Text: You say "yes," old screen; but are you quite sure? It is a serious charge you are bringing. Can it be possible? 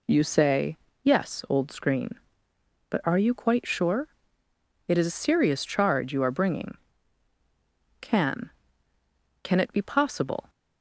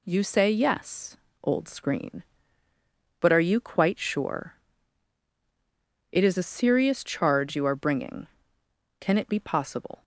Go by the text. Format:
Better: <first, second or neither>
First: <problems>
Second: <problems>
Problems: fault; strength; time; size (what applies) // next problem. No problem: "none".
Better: second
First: pauses between "say" and "yes"; slight; at 0.7 s; 0.26 s long // says "Can" twice; at 9.4 s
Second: none